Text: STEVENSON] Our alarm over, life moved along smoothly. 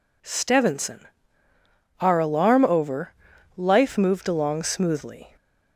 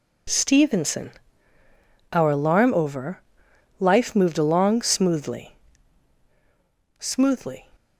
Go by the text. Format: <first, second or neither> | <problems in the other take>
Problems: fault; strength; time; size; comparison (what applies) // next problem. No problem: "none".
first | pauses between "STEVENSON" and "Our"; at 1.1 s; 1.0 s long; noticeable in the first // says "smoothly" twice; at 6.9 s